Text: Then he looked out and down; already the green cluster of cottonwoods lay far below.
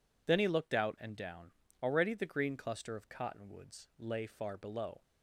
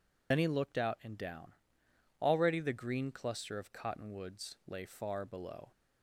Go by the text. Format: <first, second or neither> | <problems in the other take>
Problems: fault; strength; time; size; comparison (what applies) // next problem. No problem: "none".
first | loses the start of "Then"; at 0.3 s; 55 ms